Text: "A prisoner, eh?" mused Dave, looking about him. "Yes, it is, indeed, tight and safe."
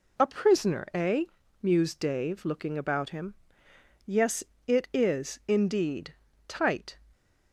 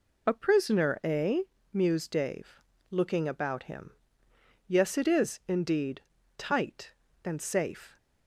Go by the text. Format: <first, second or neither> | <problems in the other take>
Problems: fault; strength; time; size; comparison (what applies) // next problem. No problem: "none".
second | stops before "and safe"; at 7.1 s